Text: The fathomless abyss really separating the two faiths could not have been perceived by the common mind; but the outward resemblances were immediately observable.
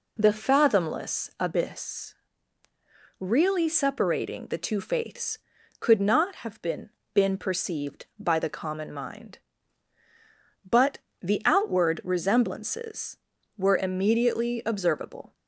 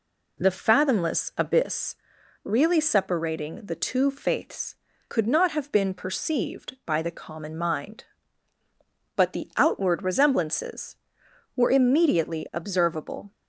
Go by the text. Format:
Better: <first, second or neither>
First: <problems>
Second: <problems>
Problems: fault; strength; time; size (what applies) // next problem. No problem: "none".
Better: second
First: pauses between "abyss" and "really"; at 2.1 s; 1.0 s long // says "been" twice; at 7.1 s // pauses between "but" and "the"; slight; at 10.9 s; 0.24 s long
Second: pauses between "abyss" and "really"; noticeable; at 1.9 s; 0.48 s long